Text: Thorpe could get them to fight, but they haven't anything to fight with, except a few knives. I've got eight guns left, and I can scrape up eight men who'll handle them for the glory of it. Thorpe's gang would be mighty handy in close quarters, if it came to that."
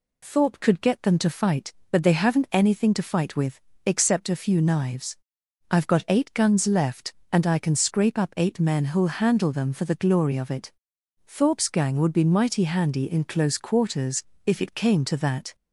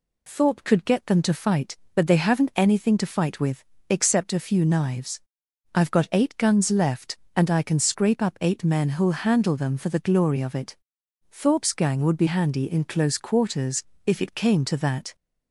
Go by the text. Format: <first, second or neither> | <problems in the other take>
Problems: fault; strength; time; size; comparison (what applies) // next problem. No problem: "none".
first | skips "mighty"; at 12.2 s